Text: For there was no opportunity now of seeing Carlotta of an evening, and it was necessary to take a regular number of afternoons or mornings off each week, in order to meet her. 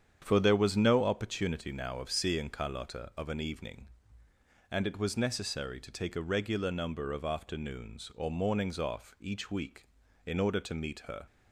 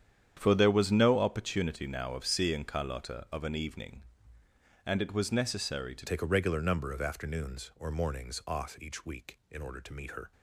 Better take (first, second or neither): first